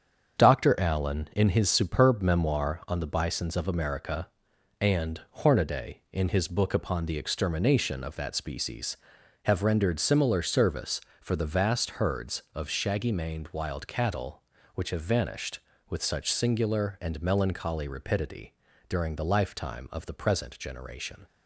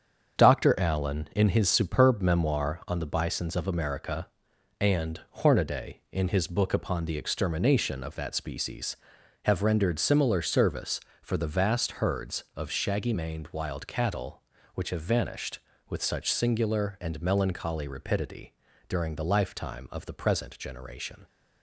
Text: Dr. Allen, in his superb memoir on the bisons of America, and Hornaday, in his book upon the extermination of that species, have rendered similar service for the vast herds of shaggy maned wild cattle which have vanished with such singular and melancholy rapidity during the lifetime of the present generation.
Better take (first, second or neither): neither